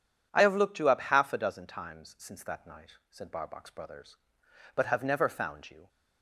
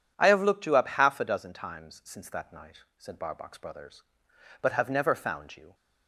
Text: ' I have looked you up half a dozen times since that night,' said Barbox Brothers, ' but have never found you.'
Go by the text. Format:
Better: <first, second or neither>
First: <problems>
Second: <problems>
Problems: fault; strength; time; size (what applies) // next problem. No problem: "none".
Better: neither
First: starts louder than the rest; strong; until 1.3 s; 9 dB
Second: starts louder than the rest; strong; until 1.1 s; 9 dB